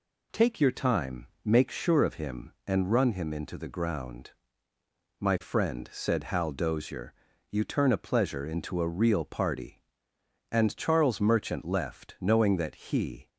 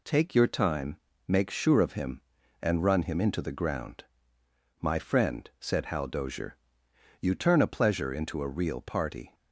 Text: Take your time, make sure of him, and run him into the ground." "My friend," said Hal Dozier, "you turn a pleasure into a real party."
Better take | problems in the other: second | goes on to say "And Charles Merchant left knowing that he"; strong; from 10.5 s on; 2.7 s long

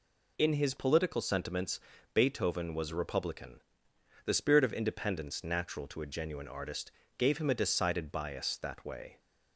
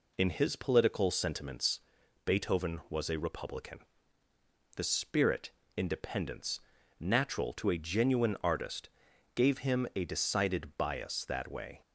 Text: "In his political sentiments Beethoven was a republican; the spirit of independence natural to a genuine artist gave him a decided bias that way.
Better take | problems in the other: first | pauses between "sentiments" and "Beethoven"; at 1.7 s; 0.44 s long; slight in the first // skips "of"; at 5.6 s // pauses between "independence" and "natural"; at 6.5 s; 0.40 s long // pauses between "artist" and "gave"; at 8.8 s; 0.44 s long; slight in the first

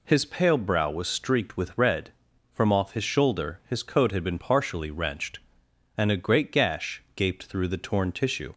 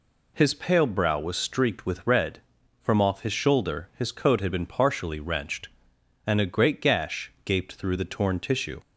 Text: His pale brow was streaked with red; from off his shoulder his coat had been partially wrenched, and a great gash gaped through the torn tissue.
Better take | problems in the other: neither | none

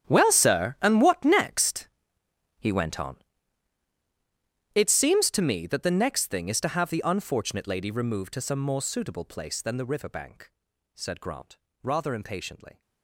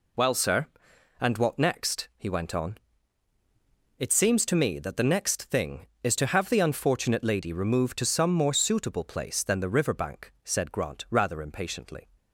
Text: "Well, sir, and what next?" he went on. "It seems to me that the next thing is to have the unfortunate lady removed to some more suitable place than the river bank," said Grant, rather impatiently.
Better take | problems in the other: second | gets quieter; strong; throughout; 17.5 dB

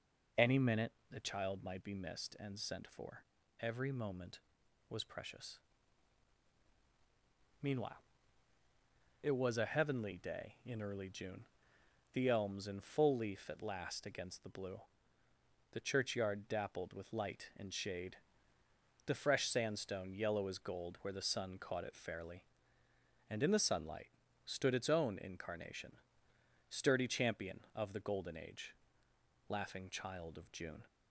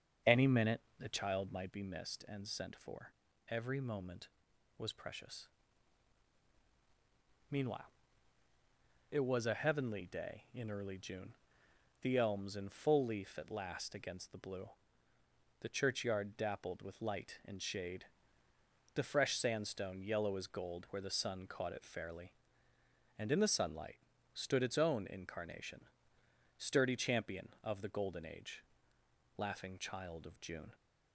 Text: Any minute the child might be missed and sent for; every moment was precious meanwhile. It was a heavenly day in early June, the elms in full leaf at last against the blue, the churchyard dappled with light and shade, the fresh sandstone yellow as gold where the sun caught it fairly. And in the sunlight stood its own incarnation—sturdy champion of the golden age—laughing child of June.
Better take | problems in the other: first | starts louder than the rest; until 1.8 s; 6.5 dB // pauses between "minute" and "the"; slight; at 0.7 s; 0.18 s long; slight in the first // pauses between "precious" and "meanwhile"; strong; at 5.4 s; 2.0 s long; strong in the first // pauses between "sunlight" and "stood"; slight; at 23.9 s; 0.36 s long; slight in the first

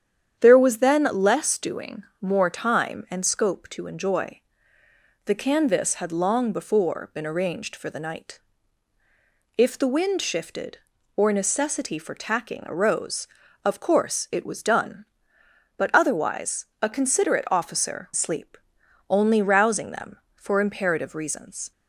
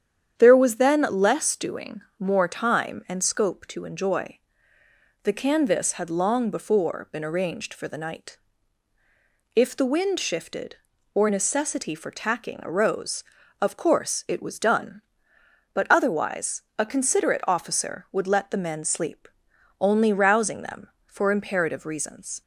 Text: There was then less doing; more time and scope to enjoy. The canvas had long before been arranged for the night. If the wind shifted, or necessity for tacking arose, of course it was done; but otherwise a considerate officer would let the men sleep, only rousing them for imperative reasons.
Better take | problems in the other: second | starts louder than the rest; strong; until 1.4 s; 9 dB; strong in the second // pauses between "otherwise" and "a"; slight; at 16.6 s; 0.18 s long; slight in the second // skips "would let the men"; at 18.1 s

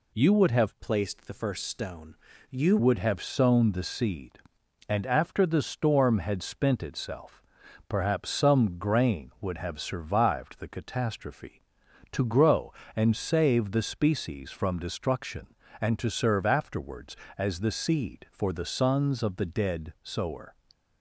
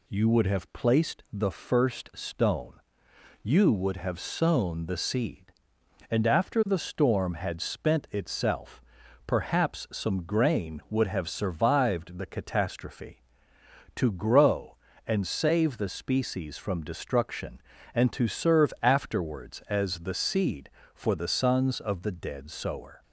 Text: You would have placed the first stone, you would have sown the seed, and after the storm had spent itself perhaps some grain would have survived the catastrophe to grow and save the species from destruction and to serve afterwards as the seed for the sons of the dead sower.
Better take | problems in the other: second | changes voice from "placed" to "you"; from 0.8 to 2.7 s; 1.9 s long // pauses between "itself" and "perhaps"; noticeable; at 7.4 s; 0.48 s long; noticeable in the second

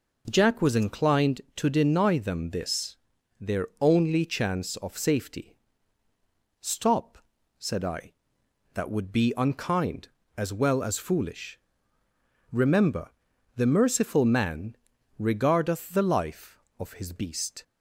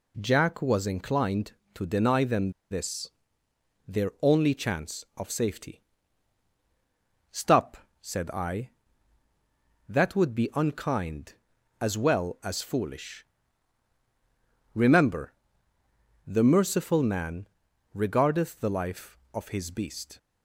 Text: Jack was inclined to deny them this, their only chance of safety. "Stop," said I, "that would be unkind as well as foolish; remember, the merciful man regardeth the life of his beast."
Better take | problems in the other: first | pauses between "them" and "this"; slight; at 2.5 s; 0.19 s long // pauses between "man" and "regardeth"; noticeable; at 17.4 s; 0.48 s long; also in the first

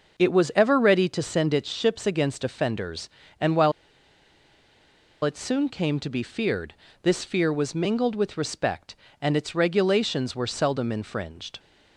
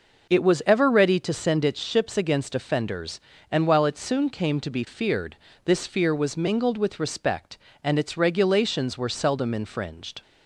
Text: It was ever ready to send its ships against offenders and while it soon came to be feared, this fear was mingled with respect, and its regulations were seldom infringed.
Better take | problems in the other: second | pauses between "while" and "it"; strong; at 3.7 s; 1.5 s long

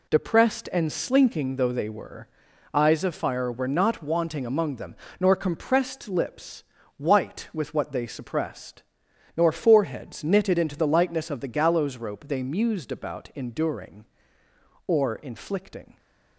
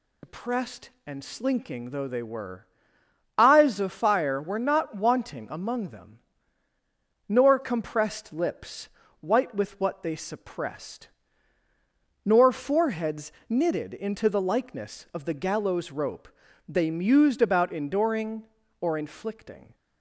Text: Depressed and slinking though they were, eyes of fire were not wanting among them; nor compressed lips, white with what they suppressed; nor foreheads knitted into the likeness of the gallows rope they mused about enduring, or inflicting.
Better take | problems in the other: first | loses the start of "Depressed"; at 0.2 s; 65 ms // pauses between "foreheads" and "knitted"; slight; at 13.3 s; 0.16 s long // pauses between "rope" and "they"; at 16.2 s; 0.40 s long

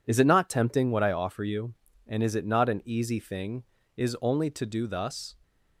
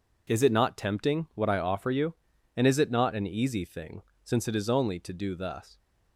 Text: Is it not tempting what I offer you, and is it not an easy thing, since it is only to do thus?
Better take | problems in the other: second | skips "since it"; at 3.8 s

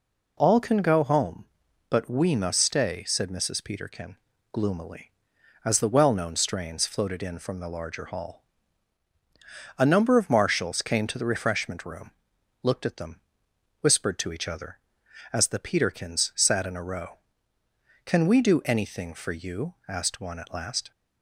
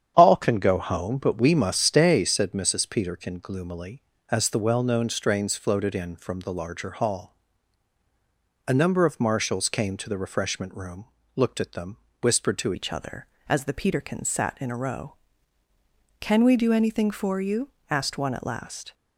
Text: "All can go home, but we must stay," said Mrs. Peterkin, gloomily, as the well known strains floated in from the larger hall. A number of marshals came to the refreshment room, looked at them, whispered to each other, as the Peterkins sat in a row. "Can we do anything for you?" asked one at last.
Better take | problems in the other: first | starts louder than the rest; strong; until 1.1 s; 8.5 dB // changes voice at "each"; from 12.7 s on; 6.2 s long

